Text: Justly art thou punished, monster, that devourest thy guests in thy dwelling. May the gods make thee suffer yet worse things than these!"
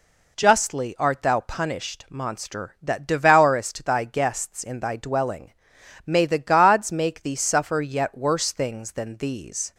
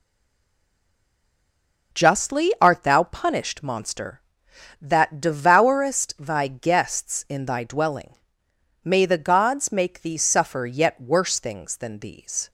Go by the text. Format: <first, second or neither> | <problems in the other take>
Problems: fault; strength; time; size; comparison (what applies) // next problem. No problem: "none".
first | stays silent before the first word; noticeable; until 1.9 s; 1.9 s long